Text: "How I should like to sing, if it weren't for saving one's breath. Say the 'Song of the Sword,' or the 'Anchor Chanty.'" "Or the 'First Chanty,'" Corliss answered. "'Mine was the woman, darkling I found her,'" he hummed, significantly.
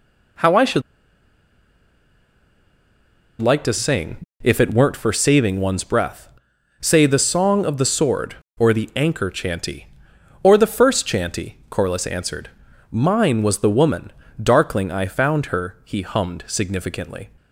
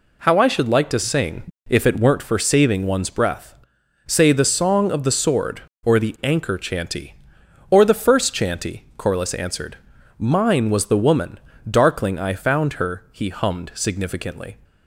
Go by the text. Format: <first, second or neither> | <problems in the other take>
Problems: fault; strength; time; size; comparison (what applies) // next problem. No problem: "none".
second | pauses between "should" and "like"; strong; at 0.8 s; 2.6 s long